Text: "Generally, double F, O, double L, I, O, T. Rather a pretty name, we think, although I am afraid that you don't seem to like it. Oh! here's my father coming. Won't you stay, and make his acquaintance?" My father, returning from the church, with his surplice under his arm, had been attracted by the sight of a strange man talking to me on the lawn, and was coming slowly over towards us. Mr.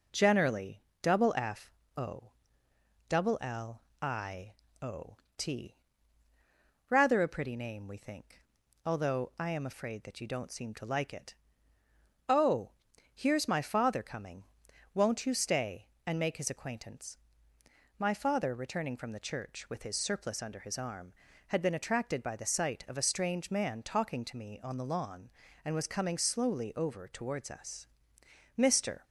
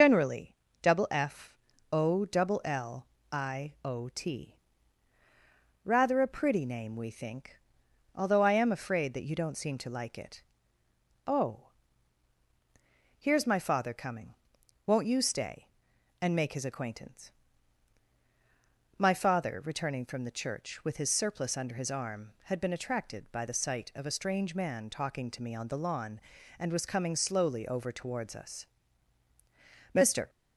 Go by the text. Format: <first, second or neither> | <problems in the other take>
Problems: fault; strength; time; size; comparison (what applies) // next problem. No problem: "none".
first | loses the start of "Generally"; at 0.0 s; 105 ms